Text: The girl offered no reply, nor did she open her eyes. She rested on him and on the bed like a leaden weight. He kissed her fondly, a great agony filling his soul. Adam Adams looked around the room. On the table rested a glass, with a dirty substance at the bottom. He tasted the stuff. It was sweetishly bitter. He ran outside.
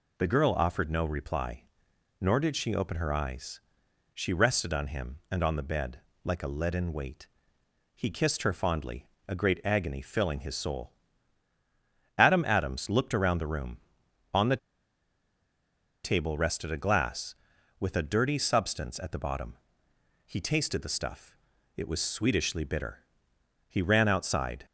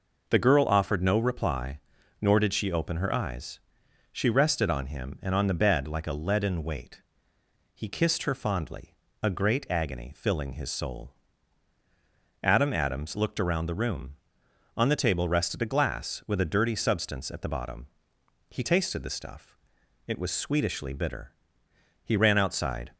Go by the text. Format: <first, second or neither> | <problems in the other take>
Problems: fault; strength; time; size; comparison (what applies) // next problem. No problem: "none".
second | pauses between "bed" and "like"; slight; at 5.9 s; 0.26 s long // pauses between "the" and "table"; strong; at 14.5 s; 1.4 s long